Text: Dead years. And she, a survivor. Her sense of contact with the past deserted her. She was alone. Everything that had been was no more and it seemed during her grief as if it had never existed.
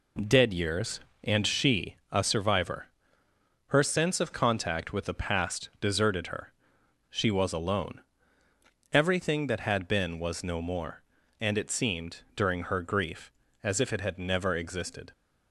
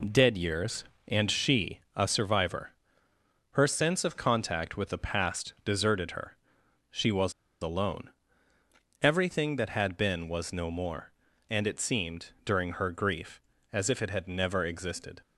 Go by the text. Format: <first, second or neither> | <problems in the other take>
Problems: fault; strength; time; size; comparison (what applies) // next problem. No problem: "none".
first | pauses between "was" and "alone"; slight; at 7.3 s; 0.29 s long // pauses between "seemed" and "during"; slight; at 12.2 s; 0.16 s long; slight in the first